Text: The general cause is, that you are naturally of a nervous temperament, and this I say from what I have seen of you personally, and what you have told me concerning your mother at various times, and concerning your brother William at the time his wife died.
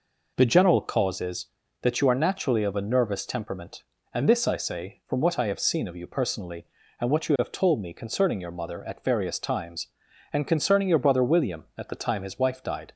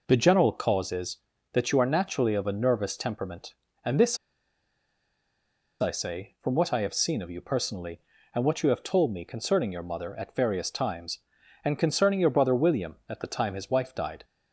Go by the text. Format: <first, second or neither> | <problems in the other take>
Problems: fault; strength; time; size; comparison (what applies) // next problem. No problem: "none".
first | pauses between "this" and "I"; strong; at 4.1 s; 1.6 s long